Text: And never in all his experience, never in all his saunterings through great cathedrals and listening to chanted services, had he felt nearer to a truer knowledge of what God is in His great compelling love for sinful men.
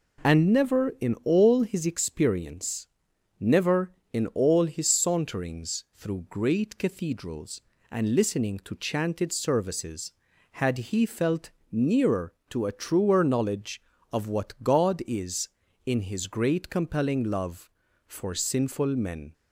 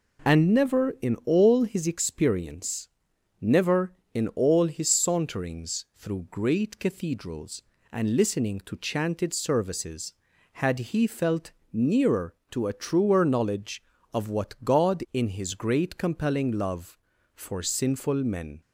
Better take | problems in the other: first | pauses between "felt" and "nearer"; slight; at 11.5 s; 0.20 s long; slight in the first // skips "is"; at 15.0 s

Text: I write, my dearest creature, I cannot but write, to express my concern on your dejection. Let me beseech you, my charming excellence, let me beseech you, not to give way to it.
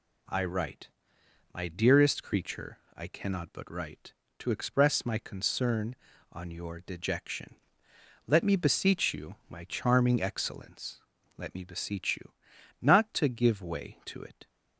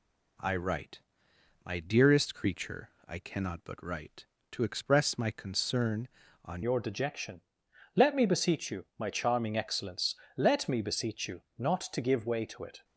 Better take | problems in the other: first | changes voice at "your"; from 6.6 s on; 6.2 s long

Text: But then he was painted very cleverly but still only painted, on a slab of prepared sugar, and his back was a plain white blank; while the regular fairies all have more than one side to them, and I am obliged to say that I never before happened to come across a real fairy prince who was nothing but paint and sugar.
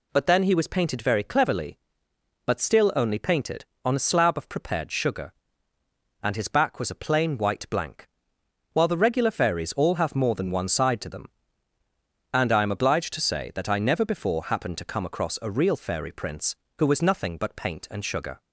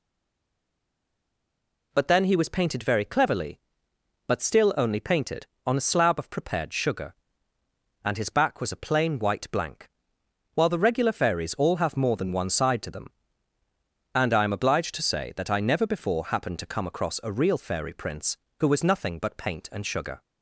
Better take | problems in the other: first | stays silent before the first word; noticeable; until 1.9 s; 1.9 s long

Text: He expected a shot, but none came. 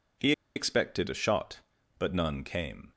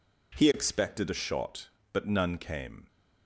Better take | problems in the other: second | pauses between "He" and "expected"; slight; at 0.3 s; 0.23 s long

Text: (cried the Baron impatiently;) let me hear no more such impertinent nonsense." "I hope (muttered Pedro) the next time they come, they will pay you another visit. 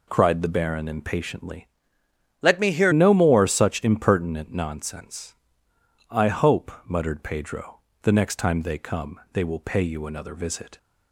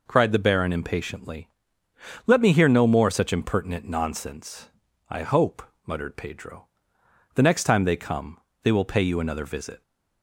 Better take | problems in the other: second | changes voice from "let" to "hear"; from 2.4 to 2.9 s; 0.5 s long

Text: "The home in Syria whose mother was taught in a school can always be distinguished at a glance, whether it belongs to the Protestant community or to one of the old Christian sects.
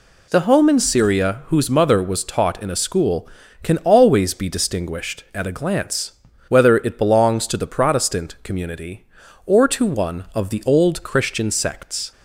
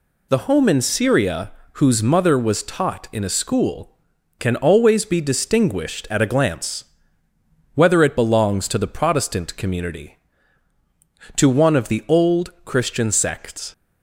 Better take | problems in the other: first | pauses between "Syria" and "whose"; slight; at 1.5 s; 0.22 s long // skips "or"; at 10.7 s

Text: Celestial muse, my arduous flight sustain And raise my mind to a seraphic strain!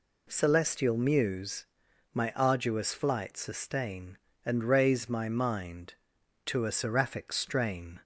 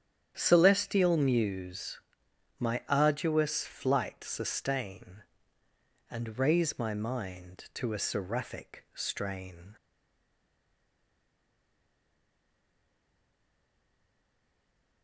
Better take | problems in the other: first | starts louder than the rest; strong; until 1.3 s; 9.5 dB // stays silent after the last word; strong; from 9.7 s on; 5.3 s long

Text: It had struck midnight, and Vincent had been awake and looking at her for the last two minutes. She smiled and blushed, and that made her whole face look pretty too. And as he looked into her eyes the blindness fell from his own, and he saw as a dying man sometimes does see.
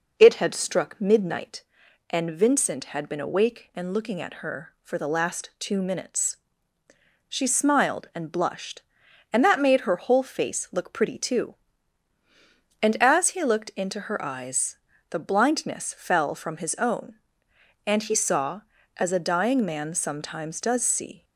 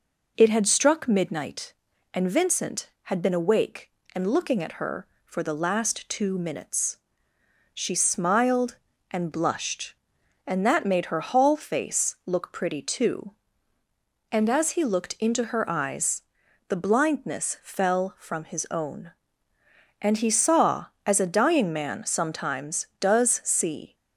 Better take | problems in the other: first | says "hall" for "whole"; at 11.2 s // pauses between "eyes" and "the"; noticeable; at 16.2 s; 0.46 s long; slight in the first

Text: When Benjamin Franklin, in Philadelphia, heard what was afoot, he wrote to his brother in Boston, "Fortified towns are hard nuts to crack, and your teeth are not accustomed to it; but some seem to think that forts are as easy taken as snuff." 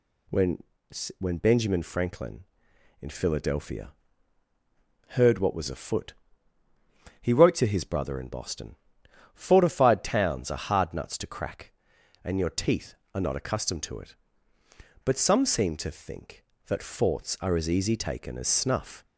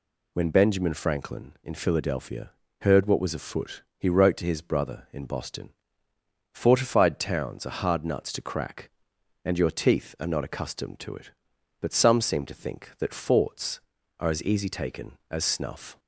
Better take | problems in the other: second | says "When" twice; at 1.1 s

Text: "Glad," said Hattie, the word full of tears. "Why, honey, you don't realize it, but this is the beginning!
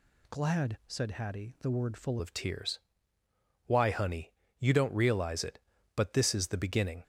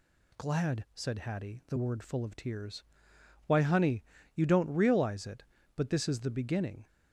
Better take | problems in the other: second | changes voice at "of"; from 2.2 s on; 4.8 s long

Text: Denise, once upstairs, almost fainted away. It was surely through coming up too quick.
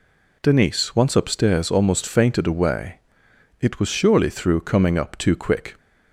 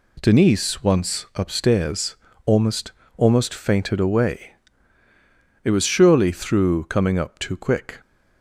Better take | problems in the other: first | says "almost" twice; at 3.1 s

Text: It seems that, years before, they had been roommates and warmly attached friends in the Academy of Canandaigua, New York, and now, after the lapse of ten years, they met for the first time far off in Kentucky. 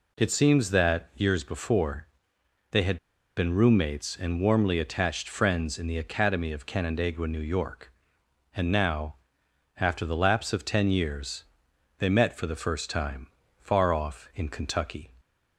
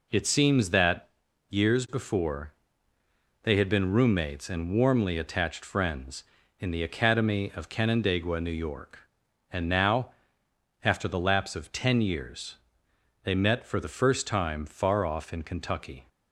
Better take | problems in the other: second | pauses between "had" and "been"; at 2.9 s; 0.38 s long // pauses between "time" and "far"; slight; at 13.2 s; 0.34 s long

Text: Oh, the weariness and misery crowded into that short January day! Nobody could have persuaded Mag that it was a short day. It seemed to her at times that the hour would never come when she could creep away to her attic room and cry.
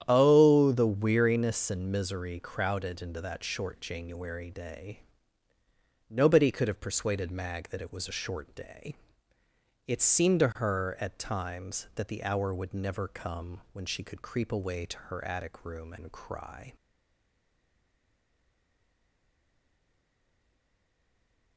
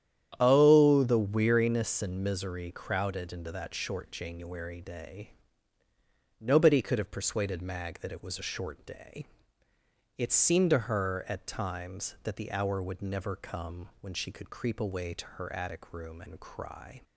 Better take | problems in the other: second | starts louder than the rest; strong; until 1.0 s; 10 dB; strong in the second // stays silent after the last word; strong; from 16.7 s on; 4.8 s long

